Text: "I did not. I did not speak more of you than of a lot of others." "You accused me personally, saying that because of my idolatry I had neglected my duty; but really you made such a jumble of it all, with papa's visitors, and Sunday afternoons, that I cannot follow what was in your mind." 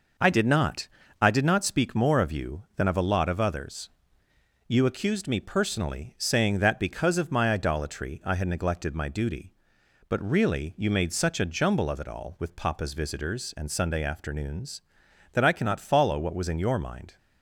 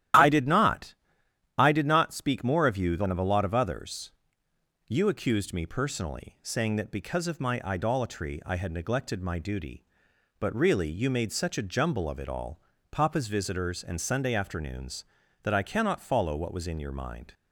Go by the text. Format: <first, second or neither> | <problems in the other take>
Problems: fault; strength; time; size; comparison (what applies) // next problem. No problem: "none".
first | starts louder than the rest; strong; until 1.8 s; 12 dB // skips "with"; at 12.7 s